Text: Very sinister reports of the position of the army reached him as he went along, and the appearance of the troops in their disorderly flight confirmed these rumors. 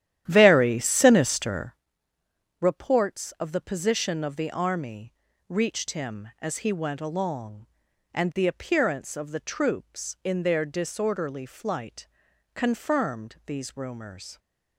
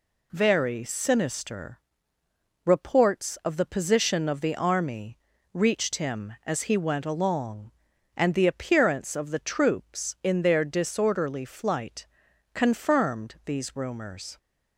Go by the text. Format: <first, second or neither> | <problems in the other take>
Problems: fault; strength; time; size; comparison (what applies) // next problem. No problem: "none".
second | starts louder than the rest; strong; until 1.8 s; 11.5 dB // pauses between "sinister" and "reports"; noticeable; at 1.7 s; 0.84 s long; noticeable in the second // pauses between "army" and "reached"; slight; at 5.1 s; 0.34 s long; slight in the second // pauses between "flight" and "confirmed"; at 12.0 s; 0.44 s long; also in the second